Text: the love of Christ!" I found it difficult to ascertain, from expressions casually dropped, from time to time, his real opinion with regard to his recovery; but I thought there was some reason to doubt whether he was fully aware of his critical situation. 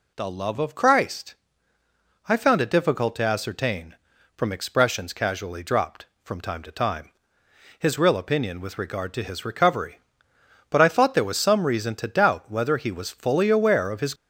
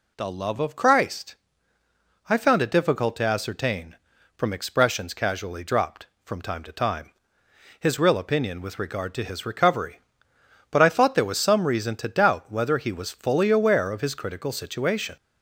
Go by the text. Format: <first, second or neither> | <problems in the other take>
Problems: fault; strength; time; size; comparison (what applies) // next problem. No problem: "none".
second | stops before "critical situation"; at 14.1 s